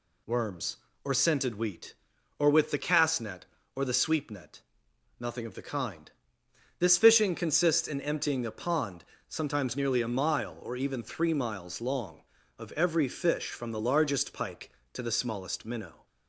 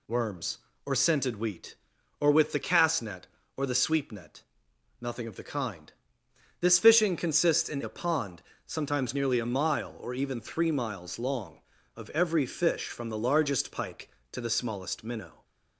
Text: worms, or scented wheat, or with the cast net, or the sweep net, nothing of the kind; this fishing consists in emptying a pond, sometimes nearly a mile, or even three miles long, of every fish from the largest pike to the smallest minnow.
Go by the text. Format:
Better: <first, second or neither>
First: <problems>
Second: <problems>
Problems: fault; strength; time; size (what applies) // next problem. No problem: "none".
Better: first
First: none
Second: skips "emptying"; at 7.8 s